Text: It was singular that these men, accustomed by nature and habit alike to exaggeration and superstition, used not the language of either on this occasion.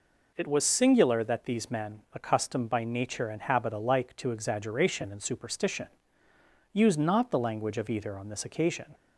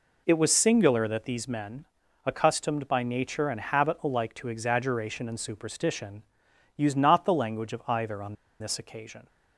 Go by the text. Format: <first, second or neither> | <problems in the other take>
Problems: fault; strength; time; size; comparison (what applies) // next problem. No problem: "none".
first | pauses between "on" and "this"; slight; at 8.3 s; 0.25 s long